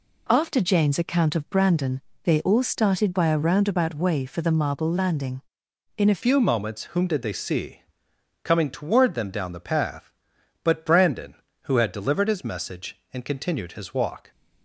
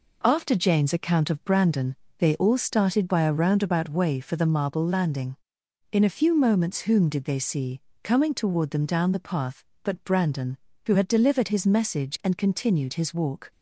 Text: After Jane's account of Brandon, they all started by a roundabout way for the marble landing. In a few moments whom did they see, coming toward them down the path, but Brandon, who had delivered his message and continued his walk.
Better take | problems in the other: second | changes voice at "few"; from 6.2 s on; 8.1 s long

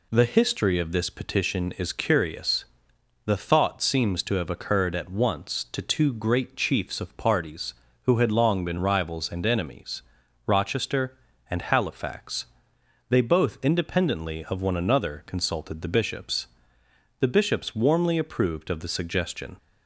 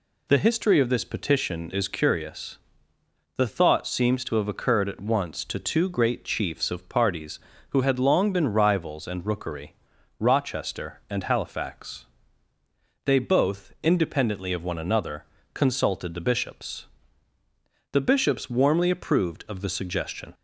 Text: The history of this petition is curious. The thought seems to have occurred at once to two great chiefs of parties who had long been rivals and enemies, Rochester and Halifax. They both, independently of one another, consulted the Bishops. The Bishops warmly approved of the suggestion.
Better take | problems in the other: first | says "rookery" for "enemies"; at 9.2 s

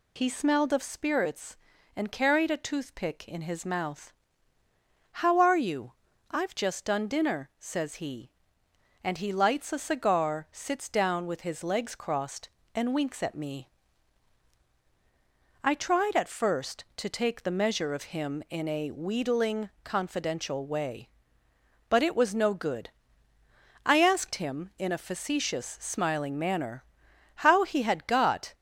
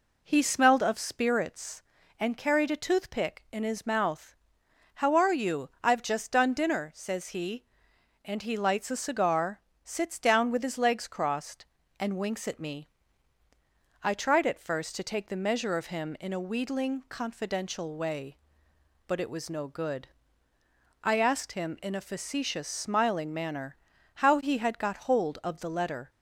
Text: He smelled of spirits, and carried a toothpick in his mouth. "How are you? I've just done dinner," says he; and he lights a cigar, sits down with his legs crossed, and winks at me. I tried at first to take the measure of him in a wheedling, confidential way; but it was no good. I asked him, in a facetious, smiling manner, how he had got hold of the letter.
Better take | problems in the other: second | stops before "hold of the letter"; at 28.5 s

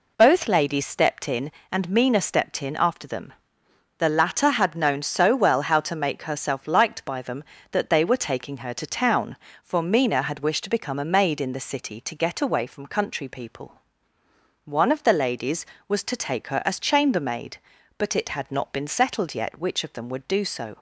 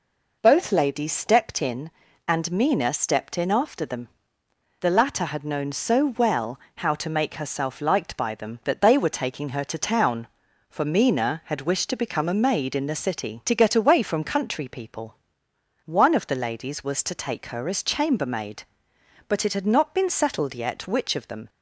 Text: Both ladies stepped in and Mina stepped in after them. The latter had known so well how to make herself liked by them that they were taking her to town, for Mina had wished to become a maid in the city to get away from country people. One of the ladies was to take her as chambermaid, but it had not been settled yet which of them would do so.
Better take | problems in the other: first | pauses between "well" and "how"; slight; at 6.5 s; 0.18 s long // stops before "would do so"; at 21.4 s

